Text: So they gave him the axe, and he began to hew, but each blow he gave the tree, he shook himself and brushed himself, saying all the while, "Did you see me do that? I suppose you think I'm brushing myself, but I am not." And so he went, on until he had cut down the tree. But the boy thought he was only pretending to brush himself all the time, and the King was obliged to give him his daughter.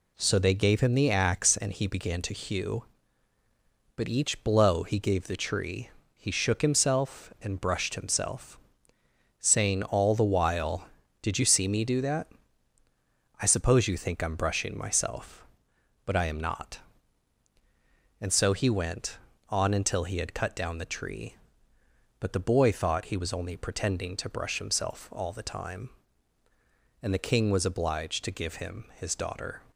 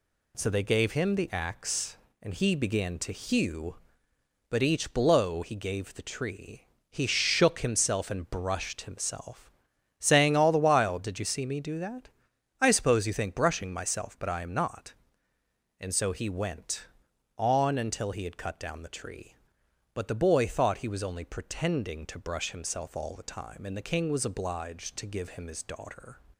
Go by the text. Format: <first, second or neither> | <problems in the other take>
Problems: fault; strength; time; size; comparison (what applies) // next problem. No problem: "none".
first | skips "I'm"; at 13.3 s